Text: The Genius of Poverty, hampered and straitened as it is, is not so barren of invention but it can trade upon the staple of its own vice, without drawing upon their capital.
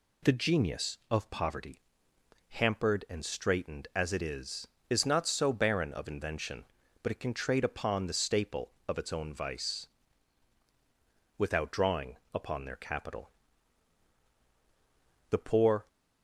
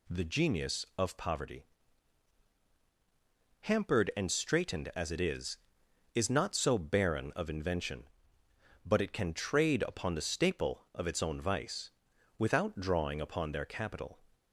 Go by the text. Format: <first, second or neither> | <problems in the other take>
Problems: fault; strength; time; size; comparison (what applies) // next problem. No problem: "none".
second | pauses between "drawing" and "upon"; slight; at 12.1 s; 0.18 s long // goes on to say "The poor"; from 15.3 s on; 0.56 s long